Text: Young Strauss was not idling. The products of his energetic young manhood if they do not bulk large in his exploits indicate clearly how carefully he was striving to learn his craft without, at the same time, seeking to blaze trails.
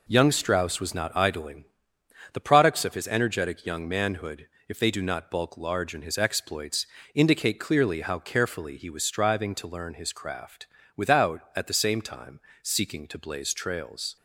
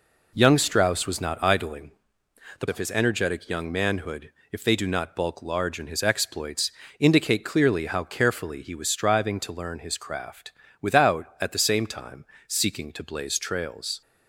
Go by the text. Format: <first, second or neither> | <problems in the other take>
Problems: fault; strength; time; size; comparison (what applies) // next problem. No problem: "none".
first | skips "products"; at 2.6 s // pauses between "manhood" and "if"; slight; at 4.3 s; 0.22 s long; slight in the first // pauses between "exploits" and "indicate"; slight; at 6.7 s; 0.30 s long; slight in the first // pauses between "craft" and "without"; slight; at 10.5 s; 0.28 s long; slight in the first